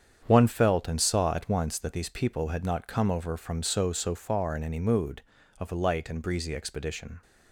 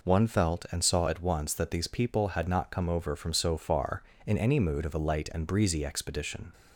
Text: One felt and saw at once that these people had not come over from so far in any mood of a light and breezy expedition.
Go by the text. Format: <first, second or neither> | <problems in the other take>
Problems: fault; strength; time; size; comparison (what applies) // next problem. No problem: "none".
second | starts louder than the rest; strong; until 1.2 s; 8 dB // says "so" twice; at 3.9 s